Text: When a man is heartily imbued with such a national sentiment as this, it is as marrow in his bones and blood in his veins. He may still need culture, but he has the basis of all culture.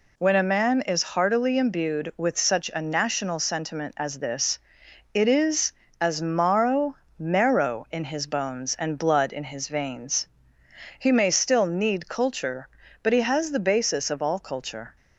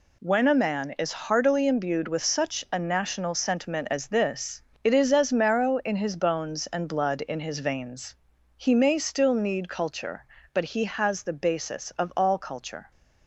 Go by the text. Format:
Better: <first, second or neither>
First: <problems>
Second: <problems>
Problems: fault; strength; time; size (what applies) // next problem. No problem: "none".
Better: second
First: says "marrow" twice; at 7.1 s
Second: none